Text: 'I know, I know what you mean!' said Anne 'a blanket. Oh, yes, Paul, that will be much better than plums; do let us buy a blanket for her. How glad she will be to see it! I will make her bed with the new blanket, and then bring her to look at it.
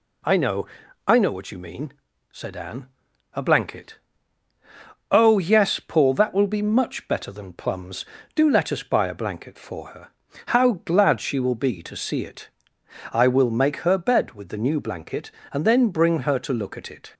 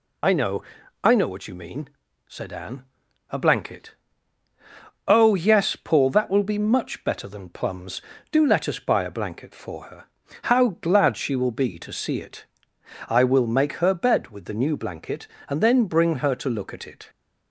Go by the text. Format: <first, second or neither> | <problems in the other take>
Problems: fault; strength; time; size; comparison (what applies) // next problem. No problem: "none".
first | loses the start of "I"; at 0.2 s; 25 ms // pauses between "Anne" and "a"; noticeable; at 2.8 s; 0.46 s long; noticeable in the first